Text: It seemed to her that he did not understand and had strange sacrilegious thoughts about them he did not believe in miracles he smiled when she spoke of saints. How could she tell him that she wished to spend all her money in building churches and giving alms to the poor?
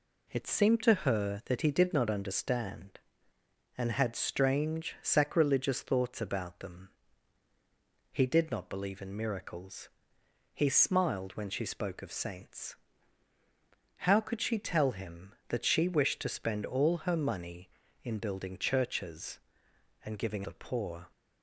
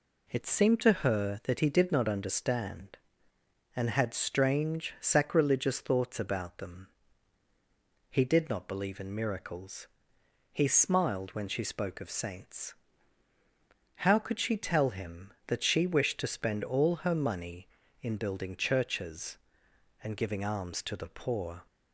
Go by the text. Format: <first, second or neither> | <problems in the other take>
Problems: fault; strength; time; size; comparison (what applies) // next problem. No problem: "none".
second | pauses between "them" and "he"; at 6.8 s; 1.2 s long; also in the second // pauses between "miracles" and "he"; noticeable; at 9.8 s; 0.66 s long; noticeable in the second // skips "alms to"; at 20.4 s